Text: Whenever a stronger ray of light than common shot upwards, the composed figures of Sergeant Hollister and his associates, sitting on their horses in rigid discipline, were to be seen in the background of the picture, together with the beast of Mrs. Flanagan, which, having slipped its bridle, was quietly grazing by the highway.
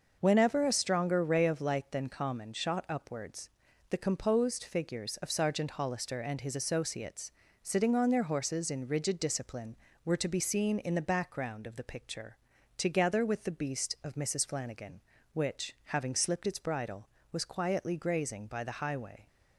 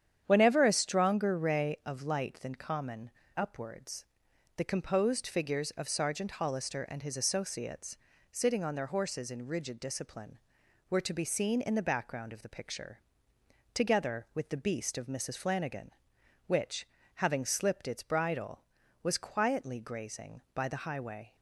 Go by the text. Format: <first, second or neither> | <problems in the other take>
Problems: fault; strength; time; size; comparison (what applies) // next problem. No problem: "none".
first | starts louder than the rest; strong; until 1.2 s; 9 dB; also in the first // skips "shot"; at 3.2 s